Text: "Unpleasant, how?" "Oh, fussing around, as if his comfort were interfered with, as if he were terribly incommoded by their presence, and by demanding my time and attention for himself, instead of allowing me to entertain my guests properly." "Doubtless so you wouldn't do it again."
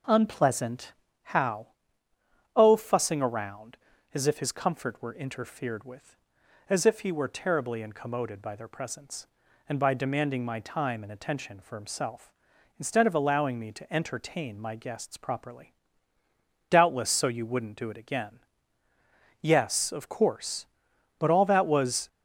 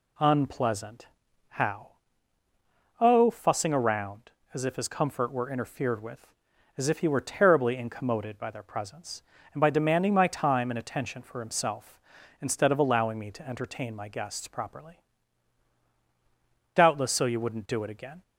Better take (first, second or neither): second